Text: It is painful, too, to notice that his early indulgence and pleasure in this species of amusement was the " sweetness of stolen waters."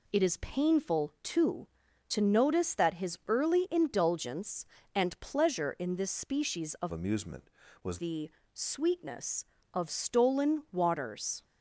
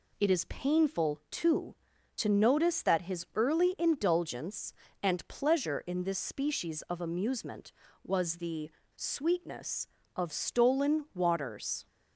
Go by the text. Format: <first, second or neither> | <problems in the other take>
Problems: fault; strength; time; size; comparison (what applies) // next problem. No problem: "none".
second | changes voice from "amusement" to "was"; from 6.9 to 7.9 s; 1.0 s long